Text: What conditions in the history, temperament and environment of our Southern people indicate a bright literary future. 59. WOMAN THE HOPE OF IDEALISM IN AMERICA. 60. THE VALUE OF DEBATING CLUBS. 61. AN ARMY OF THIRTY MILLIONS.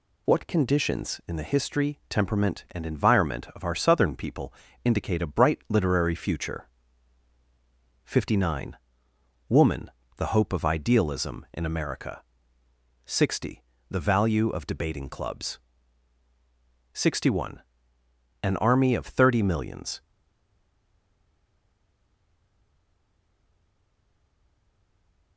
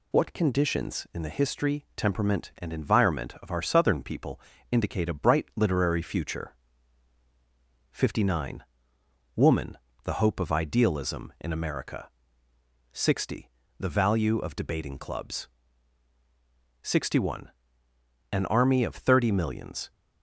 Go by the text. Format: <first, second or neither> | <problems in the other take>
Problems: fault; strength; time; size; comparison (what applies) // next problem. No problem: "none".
second | pauses between "people" and "indicate"; slight; at 4.5 s; 0.32 s long; slight in the second // pauses between "WOMAN" and "THE"; slight; at 9.9 s; 0.24 s long; slight in the second // stays silent after the last word; strong; from 20.0 s on; 5.3 s long